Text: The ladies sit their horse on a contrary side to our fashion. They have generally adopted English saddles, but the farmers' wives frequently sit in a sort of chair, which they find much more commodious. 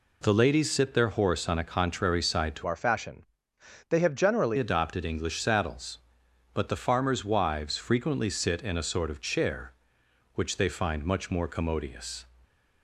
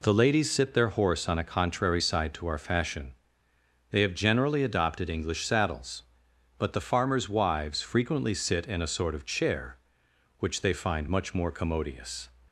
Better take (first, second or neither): second